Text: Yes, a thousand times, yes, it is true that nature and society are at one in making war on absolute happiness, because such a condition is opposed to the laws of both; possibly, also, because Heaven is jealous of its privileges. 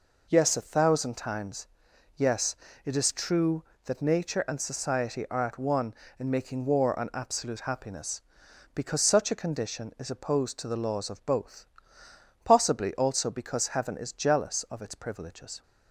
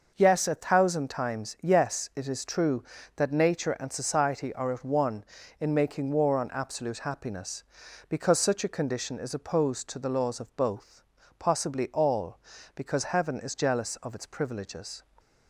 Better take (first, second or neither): first